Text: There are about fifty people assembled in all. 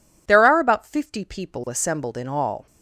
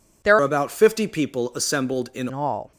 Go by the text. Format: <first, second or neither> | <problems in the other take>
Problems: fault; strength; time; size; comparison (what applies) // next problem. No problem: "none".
first | changes voice from "are" to "in"; from 0.3 to 2.2 s; 1.9 s long